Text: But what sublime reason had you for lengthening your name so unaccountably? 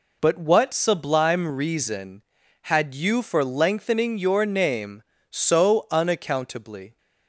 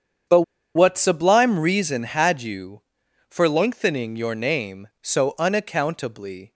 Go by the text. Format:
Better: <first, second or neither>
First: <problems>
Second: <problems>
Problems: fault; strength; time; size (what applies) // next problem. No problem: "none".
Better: first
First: none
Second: starts louder than the rest; strong; until 1.6 s; 8 dB // pauses between "But" and "what"; slight; at 0.4 s; 0.33 s long